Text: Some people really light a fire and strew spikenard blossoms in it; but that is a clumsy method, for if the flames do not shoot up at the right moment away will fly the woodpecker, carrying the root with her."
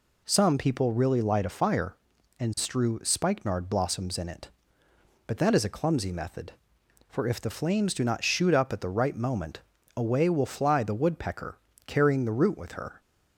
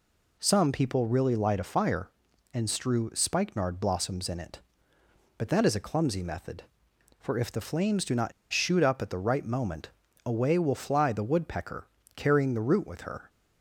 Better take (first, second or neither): first